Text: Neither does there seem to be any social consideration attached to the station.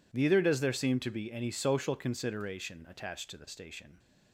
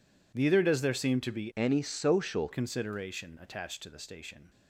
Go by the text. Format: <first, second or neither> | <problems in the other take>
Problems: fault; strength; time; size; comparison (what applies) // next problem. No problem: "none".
first | changes voice from "any" to "social"; from 1.5 to 2.4 s; 0.9 s long